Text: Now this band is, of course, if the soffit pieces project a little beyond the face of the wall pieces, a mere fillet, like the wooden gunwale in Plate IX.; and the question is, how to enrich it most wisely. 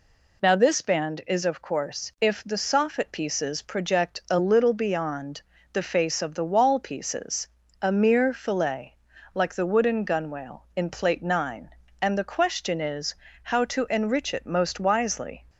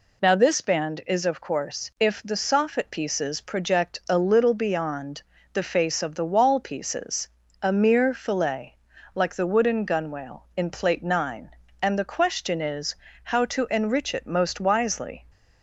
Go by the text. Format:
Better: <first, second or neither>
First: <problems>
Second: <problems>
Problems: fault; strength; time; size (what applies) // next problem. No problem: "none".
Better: neither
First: pauses between "beyond" and "the"; slight; at 5.4 s; 0.32 s long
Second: pauses between "beyond" and "the"; slight; at 5.2 s; 0.32 s long